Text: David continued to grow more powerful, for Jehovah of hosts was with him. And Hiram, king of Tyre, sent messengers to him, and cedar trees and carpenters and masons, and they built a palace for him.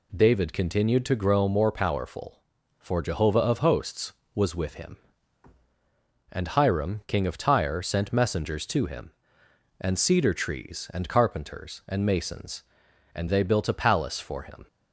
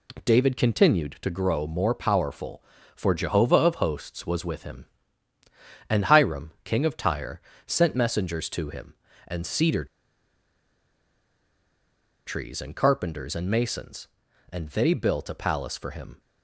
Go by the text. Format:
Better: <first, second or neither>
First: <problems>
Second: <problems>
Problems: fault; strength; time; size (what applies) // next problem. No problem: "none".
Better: first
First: none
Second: pauses between "cedar" and "trees"; strong; at 9.8 s; 2.4 s long